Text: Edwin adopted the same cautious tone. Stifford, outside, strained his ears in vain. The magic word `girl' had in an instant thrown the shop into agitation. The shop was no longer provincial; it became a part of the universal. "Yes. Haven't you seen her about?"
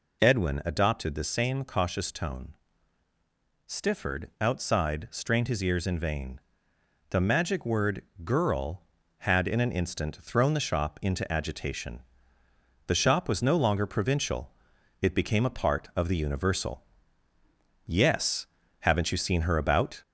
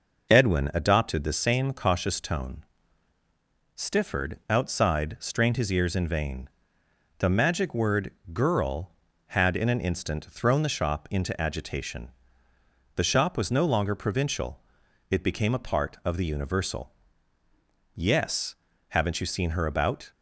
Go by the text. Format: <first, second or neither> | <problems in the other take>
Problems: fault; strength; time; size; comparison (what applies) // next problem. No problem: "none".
second | gets louder; slight; throughout; 2.5 dB // pauses between "word" and "girl"; slight; at 8.0 s; 0.22 s long; slight in the second